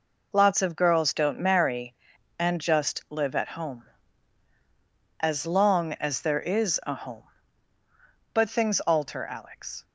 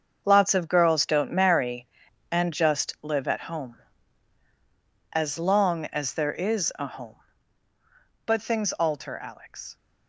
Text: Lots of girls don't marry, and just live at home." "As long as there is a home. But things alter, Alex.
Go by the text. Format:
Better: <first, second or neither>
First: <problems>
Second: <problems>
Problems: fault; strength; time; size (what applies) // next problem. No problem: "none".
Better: first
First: none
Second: gets quieter; strong; throughout; 11 dB